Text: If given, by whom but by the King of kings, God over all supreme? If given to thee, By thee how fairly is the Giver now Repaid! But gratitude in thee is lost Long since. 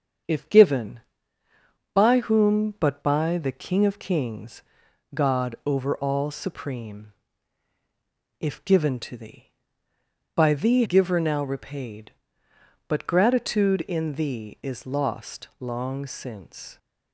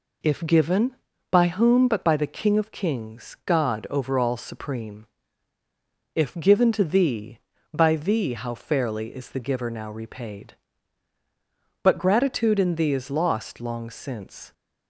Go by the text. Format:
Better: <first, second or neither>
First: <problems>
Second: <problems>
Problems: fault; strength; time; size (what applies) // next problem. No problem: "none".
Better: second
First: starts louder than the rest; strong; until 2.1 s; 7.5 dB // skips "how fairly is the"; at 10.8 s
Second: none